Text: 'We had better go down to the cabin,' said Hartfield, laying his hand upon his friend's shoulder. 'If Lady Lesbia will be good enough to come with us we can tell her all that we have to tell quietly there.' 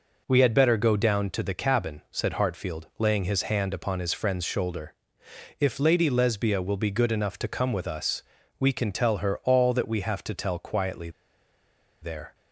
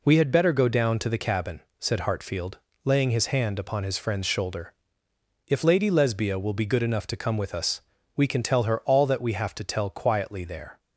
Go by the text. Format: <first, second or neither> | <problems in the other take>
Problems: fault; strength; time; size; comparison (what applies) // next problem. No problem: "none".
second | pauses between "us" and "we"; slight; at 8.2 s; 0.36 s long; slight in the second // pauses between "quietly" and "there"; noticeable; at 11.1 s; 0.91 s long